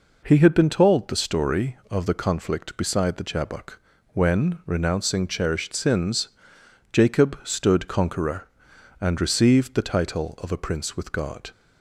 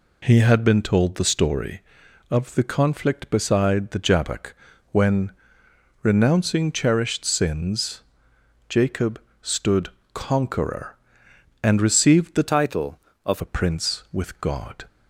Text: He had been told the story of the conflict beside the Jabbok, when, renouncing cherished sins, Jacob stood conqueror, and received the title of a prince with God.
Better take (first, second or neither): first